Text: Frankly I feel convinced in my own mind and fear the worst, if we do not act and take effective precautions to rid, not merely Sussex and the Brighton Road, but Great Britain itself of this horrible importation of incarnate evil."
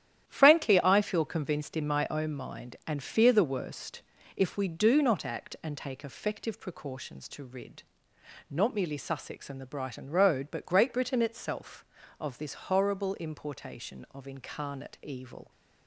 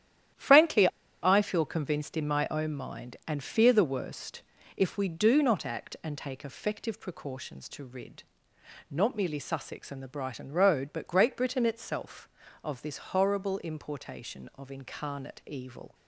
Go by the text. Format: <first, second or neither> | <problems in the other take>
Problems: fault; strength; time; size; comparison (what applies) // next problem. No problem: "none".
first | starts louder than the rest; strong; until 1.7 s; 11 dB; strong in the first // pauses between "Frankly" and "I"; slight; at 0.8 s; 0.34 s long